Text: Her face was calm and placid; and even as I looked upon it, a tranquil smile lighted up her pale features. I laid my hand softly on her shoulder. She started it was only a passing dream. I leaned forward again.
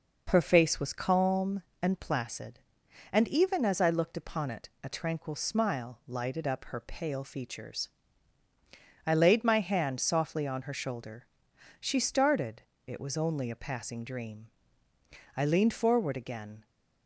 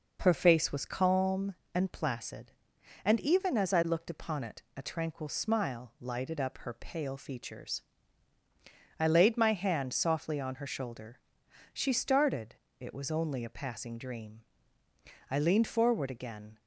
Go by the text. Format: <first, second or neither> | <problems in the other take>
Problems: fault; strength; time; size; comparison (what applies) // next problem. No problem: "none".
neither | pauses between "started" and "it"; slight; the same in both